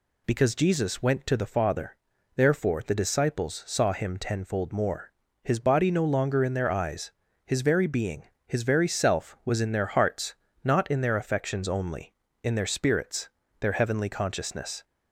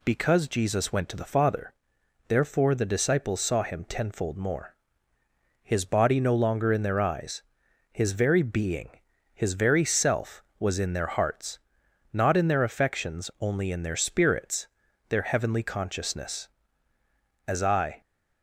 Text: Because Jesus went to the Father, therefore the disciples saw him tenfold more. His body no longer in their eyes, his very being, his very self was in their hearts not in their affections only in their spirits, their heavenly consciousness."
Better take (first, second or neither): first